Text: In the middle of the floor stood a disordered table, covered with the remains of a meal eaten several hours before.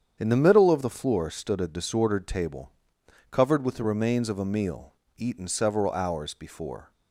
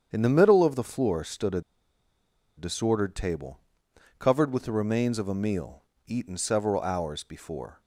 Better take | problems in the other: first | starts louder than the rest; strong; until 1.1 s; 8 dB; strong in the first // pauses between "a" and "disordered"; noticeable; at 1.6 s; 0.96 s long // pauses between "meal" and "eaten"; slight; at 5.8 s; 0.22 s long; slight in the first

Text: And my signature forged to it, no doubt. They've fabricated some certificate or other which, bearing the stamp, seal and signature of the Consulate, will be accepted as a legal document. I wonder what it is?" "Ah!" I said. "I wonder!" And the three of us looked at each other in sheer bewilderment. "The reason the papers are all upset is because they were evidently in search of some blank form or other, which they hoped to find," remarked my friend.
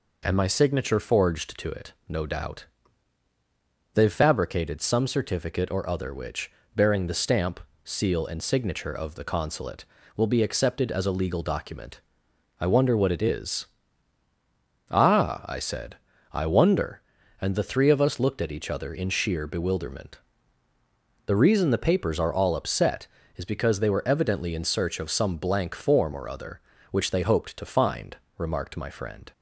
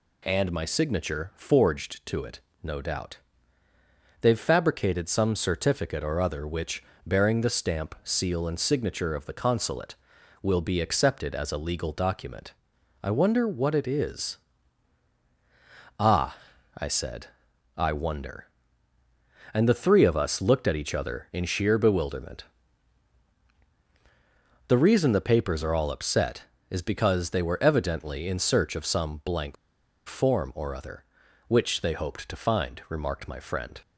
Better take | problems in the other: first | pauses between "blank" and "form"; noticeable; at 29.5 s; 0.52 s long

